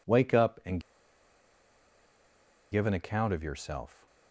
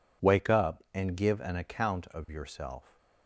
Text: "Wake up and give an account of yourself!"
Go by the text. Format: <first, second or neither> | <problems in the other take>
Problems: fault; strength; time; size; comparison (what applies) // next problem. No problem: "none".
second | pauses between "and" and "give"; strong; at 0.7 s; 1.9 s long